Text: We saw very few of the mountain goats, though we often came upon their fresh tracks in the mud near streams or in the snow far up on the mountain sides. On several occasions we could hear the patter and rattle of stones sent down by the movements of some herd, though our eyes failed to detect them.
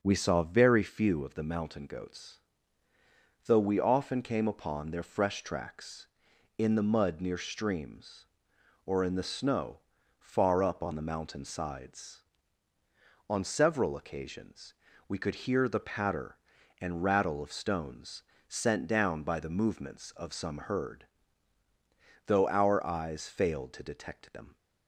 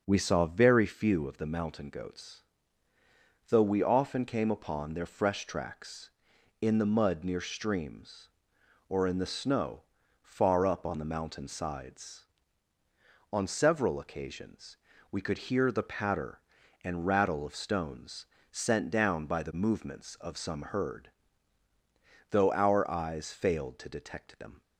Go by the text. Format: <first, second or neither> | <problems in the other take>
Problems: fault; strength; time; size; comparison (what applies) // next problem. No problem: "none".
neither | starts louder than the rest; noticeable; the same in both // pauses between "snow" and "far"; the same in both // pauses between "occasions" and "we"; slight; the same in both // pauses between "stones" and "sent"; slight; the same in both